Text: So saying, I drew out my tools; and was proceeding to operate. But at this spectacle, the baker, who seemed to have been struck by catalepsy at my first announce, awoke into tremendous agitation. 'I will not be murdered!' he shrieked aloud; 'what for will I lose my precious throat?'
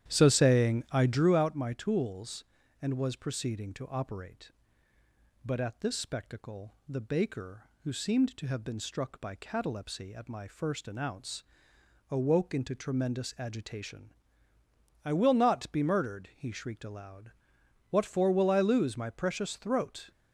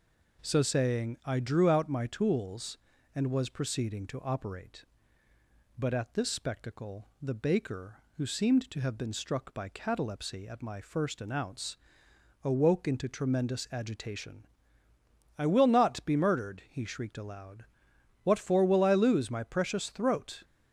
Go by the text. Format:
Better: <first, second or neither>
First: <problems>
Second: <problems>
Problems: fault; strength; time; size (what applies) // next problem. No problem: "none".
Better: second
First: starts louder than the rest; strong; until 1.4 s; 11 dB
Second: none